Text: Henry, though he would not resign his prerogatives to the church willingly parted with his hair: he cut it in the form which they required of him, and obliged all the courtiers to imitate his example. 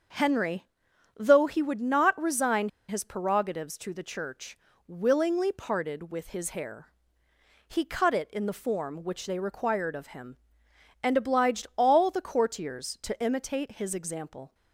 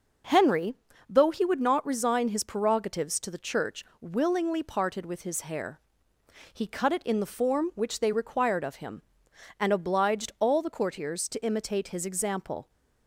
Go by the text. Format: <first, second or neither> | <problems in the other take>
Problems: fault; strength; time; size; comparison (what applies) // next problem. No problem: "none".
second | starts louder than the rest; until 1.6 s; 6.5 dB // pauses between "resign" and "his"; slight; at 2.6 s; 0.19 s long // pauses between "church" and "willingly"; slight; at 4.5 s; 0.30 s long; slight in the second